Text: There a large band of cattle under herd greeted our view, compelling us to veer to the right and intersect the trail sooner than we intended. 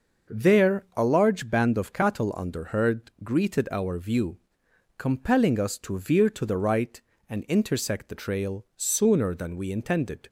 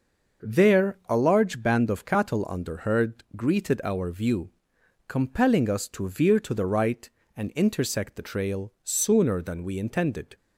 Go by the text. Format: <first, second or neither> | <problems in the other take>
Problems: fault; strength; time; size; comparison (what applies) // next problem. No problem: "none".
neither | starts louder than the rest; noticeable; the same in both